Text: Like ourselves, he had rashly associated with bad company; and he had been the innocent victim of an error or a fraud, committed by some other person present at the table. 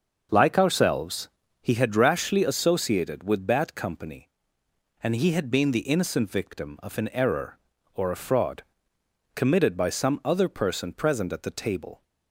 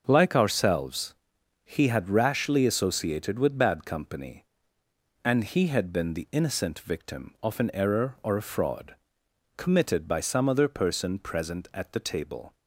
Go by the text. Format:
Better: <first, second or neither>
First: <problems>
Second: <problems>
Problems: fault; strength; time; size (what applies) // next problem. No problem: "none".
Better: neither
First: starts louder than the rest; until 1.6 s; 6 dB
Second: starts louder than the rest; until 1.0 s; 6.5 dB